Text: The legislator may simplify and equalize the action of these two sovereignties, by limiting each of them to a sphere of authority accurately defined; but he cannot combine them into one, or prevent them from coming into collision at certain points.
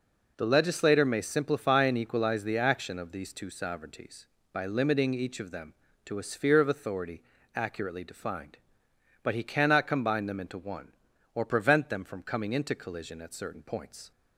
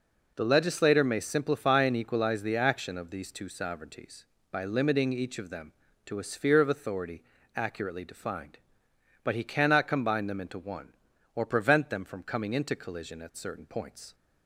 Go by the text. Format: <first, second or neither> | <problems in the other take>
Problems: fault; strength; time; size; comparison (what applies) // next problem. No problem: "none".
neither | pauses between "authority" and "accurately"; slight; the same in both